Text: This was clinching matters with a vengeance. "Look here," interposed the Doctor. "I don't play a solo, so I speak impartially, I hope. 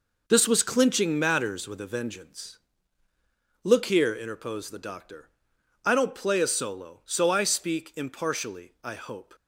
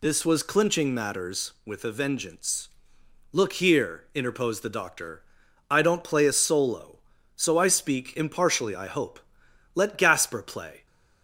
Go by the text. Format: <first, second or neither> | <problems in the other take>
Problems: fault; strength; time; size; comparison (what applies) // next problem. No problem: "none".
first | goes on to say "Let Gasper play"; noticeable; from 9.7 s on; 1.1 s long